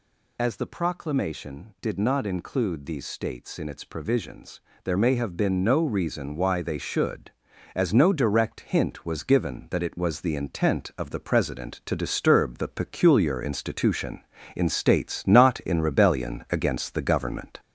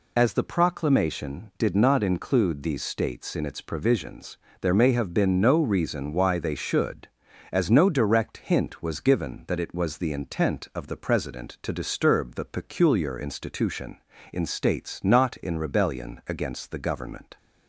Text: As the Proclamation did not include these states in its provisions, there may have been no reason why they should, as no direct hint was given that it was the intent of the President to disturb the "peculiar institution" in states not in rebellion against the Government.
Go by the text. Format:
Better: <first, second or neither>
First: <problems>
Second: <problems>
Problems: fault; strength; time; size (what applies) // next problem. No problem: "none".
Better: second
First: gets louder; throughout; 4 dB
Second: none